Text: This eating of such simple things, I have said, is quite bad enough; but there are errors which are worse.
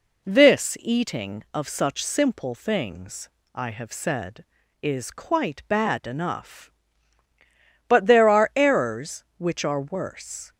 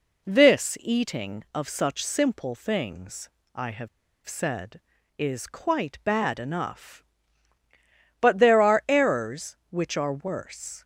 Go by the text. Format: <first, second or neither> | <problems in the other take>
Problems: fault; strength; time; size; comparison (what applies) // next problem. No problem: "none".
first | pauses between "have" and "said"; at 3.8 s; 0.38 s long